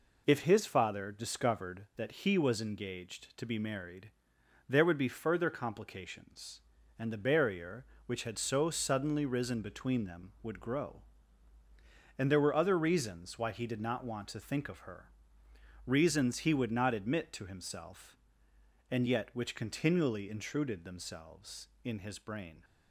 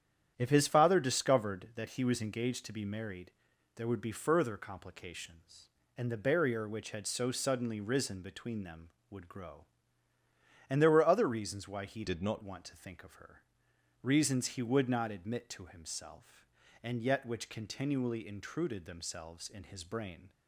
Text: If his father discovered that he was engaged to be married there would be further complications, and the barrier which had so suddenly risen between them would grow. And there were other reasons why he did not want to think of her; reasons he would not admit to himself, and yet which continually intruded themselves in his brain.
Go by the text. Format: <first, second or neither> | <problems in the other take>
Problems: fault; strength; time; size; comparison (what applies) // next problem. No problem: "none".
first | starts louder than the rest; strong; until 1.3 s; 9.5 dB // pauses between "married" and "there"; noticeable; at 3.3 s; 0.46 s long; noticeable in the first // changes voice from "did" to "not"; from 12.0 to 12.4 s; 0.4 s long